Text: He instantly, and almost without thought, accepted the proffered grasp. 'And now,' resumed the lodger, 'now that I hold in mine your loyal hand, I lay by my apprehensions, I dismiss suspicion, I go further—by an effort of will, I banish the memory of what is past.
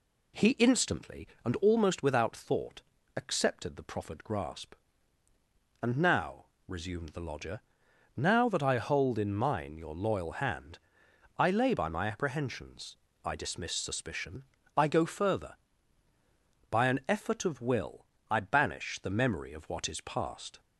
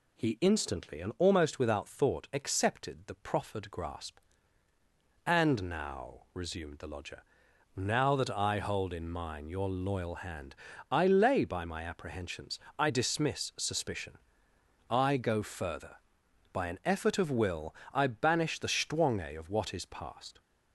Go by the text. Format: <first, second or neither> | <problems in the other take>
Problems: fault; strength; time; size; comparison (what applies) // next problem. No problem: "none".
first | says "stwange" for "memory"; at 18.6 s